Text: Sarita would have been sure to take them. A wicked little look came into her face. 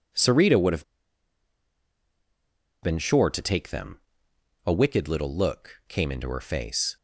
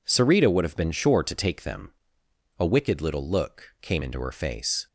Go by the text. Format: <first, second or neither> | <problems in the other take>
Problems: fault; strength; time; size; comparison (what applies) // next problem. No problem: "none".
second | pauses between "have" and "been"; strong; at 0.8 s; 1.9 s long